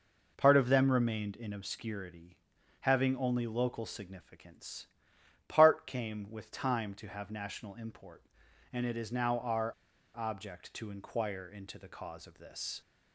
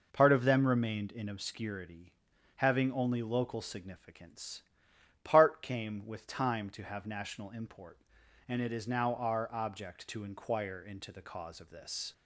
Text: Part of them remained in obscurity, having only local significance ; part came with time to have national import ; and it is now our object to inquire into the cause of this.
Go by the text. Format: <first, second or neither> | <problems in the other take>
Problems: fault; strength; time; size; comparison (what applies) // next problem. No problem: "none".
second | pauses between "our" and "object"; at 9.7 s; 0.42 s long